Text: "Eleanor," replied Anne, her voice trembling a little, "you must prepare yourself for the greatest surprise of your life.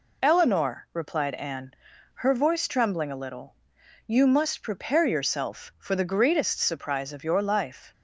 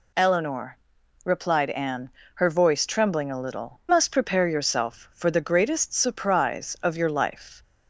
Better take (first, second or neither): first